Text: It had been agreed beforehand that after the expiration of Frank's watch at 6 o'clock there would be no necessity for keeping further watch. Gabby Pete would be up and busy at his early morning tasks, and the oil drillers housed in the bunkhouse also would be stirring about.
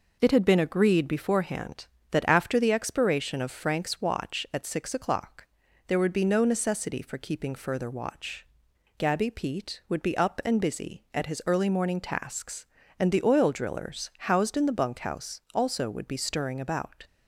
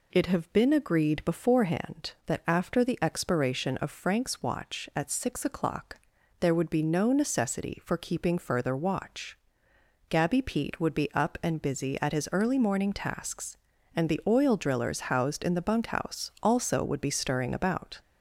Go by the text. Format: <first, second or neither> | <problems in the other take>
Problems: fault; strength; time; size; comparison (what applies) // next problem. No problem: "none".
first | says "have" for "had"; at 0.2 s // pauses between "o'clock" and "there"; at 5.9 s; 0.42 s long; also in the first